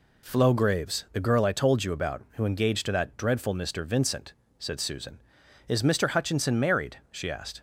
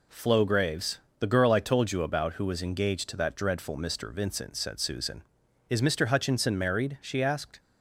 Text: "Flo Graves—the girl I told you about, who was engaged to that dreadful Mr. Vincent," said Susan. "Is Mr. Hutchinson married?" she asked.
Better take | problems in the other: second | skips "was"; at 2.4 s

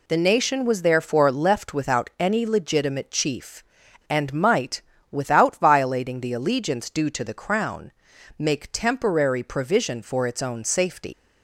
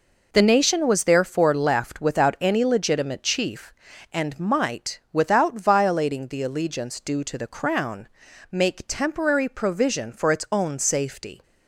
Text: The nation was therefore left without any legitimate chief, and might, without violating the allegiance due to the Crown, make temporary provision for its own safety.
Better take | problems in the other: second | leaves "safety" unfinished; at 11.1 s; 135 ms

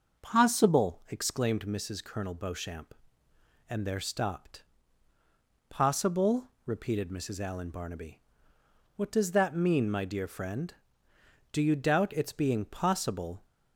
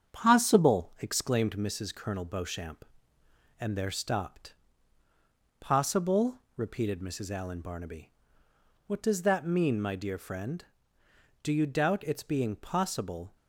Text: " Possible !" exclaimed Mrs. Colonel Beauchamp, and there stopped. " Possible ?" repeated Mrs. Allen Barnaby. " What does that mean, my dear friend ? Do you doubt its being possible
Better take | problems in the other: first | gets quieter; slight; throughout; 2.5 dB // starts louder than the rest; strong; until 1.1 s; 8 dB; also in the first

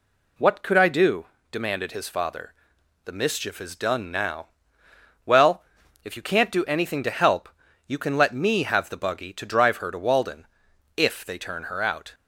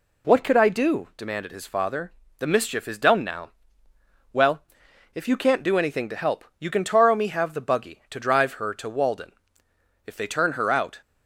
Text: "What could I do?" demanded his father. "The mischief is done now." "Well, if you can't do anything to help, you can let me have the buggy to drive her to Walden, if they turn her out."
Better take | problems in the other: first | says "taro" for "let"; at 6.8 s

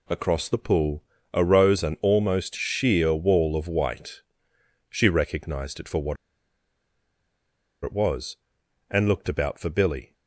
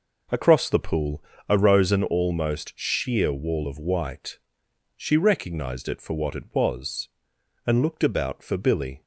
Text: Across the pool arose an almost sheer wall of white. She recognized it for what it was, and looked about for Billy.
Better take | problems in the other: second | pauses between "pool" and "arose"; slight; at 1.0 s; 0.32 s long; slight in the second // pauses between "what" and "it"; strong; at 6.1 s; 1.6 s long

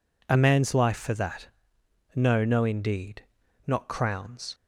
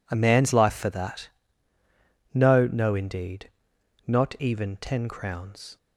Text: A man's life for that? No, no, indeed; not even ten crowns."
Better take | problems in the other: second | skips "even ten"; at 3.8 s

